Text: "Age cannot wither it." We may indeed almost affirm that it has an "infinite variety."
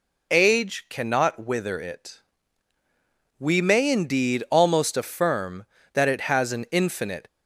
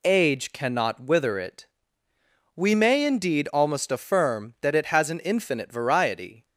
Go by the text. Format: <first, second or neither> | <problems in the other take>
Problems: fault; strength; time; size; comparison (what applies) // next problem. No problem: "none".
second | stops before "variety"; at 7.2 s